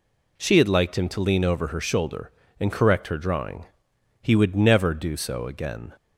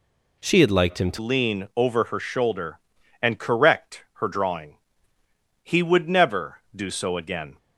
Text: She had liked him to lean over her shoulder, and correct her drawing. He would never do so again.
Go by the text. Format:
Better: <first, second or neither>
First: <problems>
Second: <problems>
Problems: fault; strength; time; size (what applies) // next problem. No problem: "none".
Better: first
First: none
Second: changes voice at "lean"; from 1.1 s on; 6.4 s long